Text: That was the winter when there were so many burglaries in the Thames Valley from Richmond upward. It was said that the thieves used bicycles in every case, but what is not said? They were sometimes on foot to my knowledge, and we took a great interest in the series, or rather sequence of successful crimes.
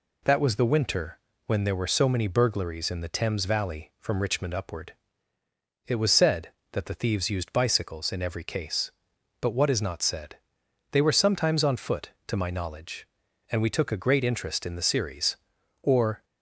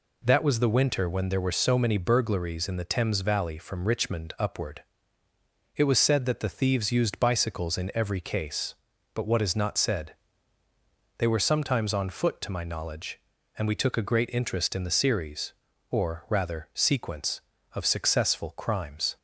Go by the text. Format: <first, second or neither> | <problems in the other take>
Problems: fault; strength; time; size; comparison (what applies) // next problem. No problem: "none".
second | pauses between "winter" and "when"; slight; at 1.1 s; 0.28 s long // stops before "rather sequence of successful crimes"; at 16.2 s